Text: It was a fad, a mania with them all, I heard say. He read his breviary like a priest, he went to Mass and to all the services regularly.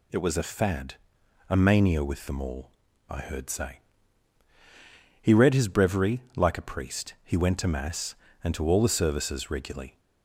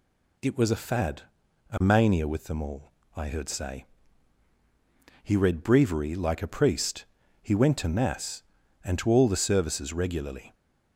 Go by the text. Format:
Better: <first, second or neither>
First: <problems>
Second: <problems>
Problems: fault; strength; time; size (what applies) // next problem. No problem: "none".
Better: first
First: none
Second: skips "his"; at 5.6 s